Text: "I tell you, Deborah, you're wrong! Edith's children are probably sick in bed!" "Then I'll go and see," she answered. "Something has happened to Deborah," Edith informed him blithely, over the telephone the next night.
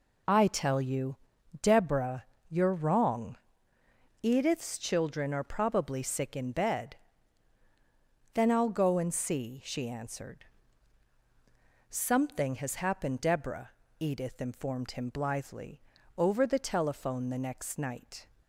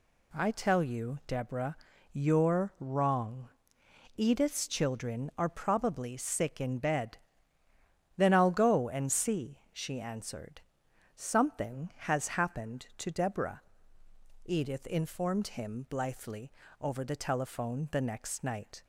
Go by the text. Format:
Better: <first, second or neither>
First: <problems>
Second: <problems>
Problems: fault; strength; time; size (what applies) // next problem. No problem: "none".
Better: second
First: skips "to"; at 13.1 s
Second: none